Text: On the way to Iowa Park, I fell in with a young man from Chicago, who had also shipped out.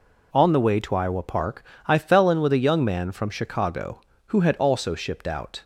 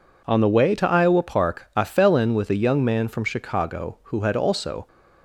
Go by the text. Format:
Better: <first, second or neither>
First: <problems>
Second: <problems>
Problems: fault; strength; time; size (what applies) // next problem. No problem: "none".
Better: first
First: none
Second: stops before "shipped out"; at 4.8 s